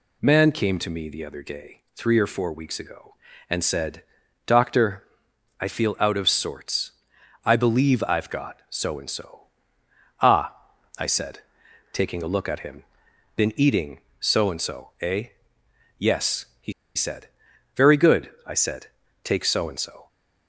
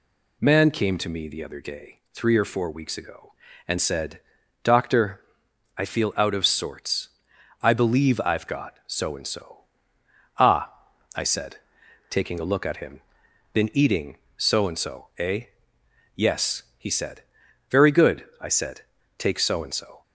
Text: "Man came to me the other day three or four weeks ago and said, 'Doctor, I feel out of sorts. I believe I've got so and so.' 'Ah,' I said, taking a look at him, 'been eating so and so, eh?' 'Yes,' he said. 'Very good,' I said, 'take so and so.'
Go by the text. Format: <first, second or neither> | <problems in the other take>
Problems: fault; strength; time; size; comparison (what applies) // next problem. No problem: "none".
second | pauses between "he" and "said"; slight; at 16.7 s; 0.23 s long